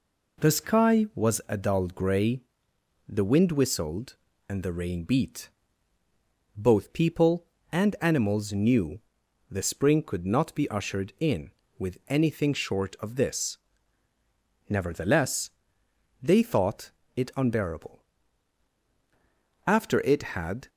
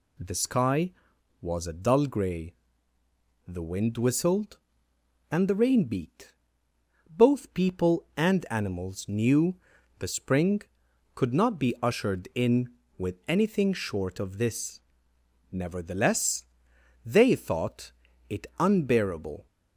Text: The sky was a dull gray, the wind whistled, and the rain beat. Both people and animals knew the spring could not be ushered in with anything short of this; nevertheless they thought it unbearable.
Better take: second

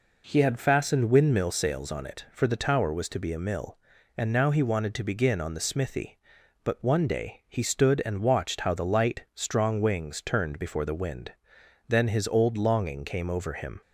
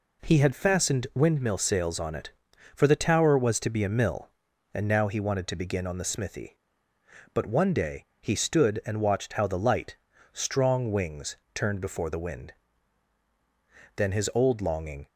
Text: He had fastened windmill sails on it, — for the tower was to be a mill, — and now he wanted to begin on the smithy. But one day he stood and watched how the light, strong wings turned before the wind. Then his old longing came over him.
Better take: first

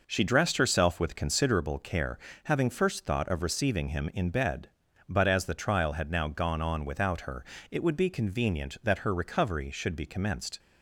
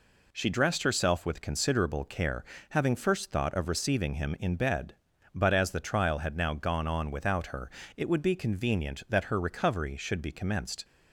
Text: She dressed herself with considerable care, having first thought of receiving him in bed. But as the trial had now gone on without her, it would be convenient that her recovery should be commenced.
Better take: second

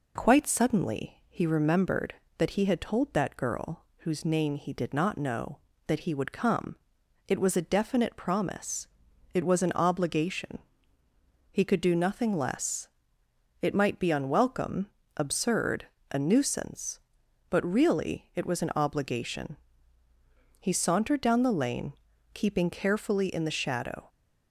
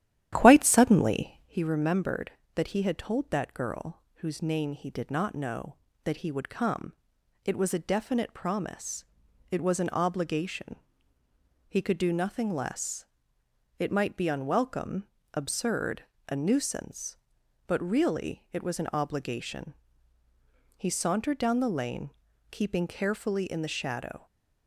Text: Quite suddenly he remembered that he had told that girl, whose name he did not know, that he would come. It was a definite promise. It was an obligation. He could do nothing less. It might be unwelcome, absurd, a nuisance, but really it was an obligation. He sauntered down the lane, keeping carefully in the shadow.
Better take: first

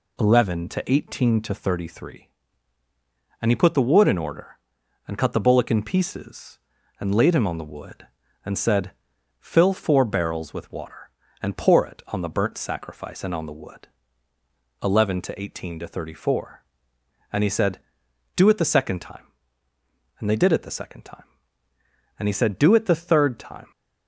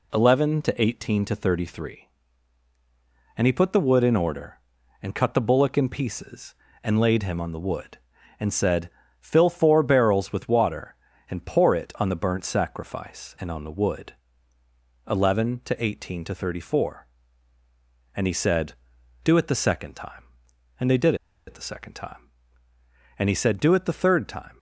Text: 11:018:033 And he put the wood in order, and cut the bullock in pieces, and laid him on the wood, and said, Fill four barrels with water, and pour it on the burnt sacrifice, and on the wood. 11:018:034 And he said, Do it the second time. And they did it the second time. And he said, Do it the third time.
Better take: first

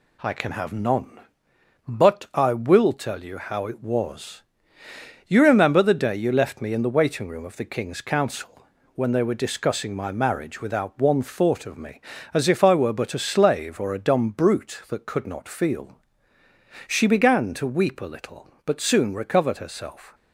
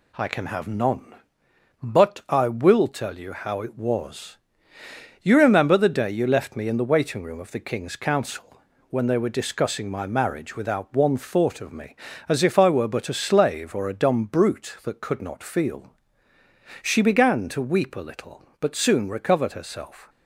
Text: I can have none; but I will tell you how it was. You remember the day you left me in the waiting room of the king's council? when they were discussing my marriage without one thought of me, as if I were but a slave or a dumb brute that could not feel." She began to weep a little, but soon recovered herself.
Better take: neither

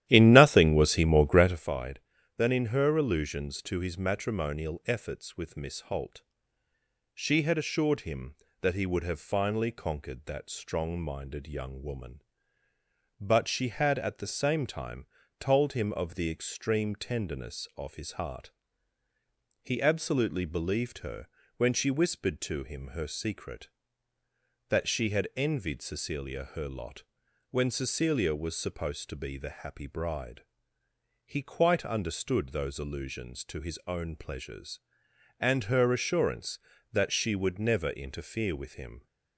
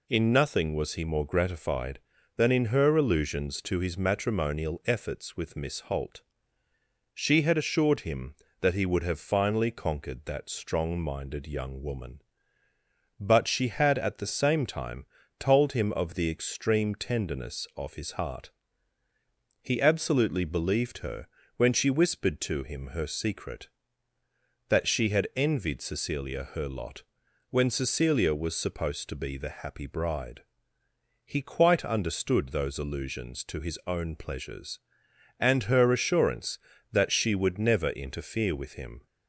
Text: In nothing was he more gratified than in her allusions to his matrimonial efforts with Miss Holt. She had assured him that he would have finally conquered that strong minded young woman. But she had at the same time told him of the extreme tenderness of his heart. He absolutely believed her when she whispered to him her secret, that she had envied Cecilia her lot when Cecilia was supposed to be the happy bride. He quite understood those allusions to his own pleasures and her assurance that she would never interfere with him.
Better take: second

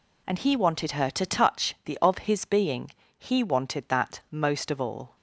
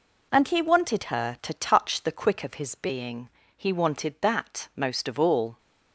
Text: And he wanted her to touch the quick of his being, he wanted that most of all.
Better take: second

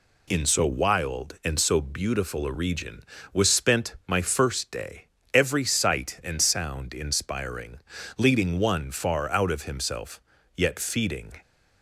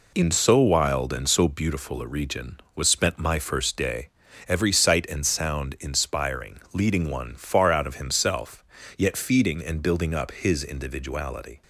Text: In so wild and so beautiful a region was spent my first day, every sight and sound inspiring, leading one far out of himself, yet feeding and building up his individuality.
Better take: second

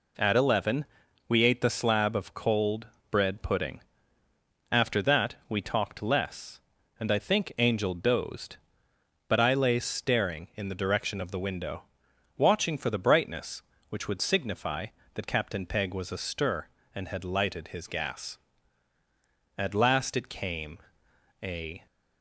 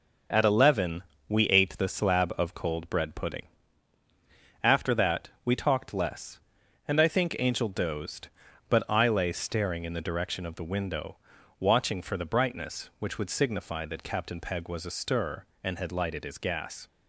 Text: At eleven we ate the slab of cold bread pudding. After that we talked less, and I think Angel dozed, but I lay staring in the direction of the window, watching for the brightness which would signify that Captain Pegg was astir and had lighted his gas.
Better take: second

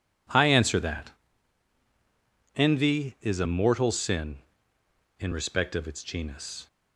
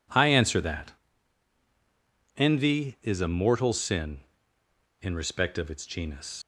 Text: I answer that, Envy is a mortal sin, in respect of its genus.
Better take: first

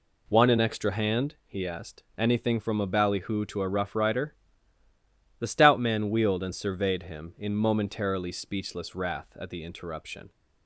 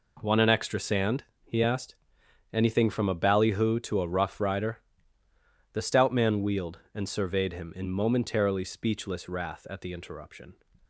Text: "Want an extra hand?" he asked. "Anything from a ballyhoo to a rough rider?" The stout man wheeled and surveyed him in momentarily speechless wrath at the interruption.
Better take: first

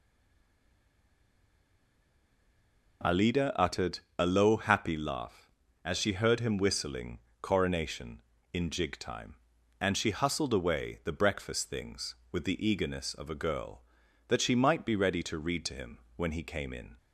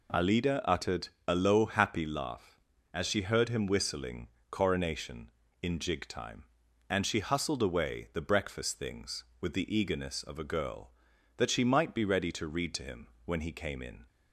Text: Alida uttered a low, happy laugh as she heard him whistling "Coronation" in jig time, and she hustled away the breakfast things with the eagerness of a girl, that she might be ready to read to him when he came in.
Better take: second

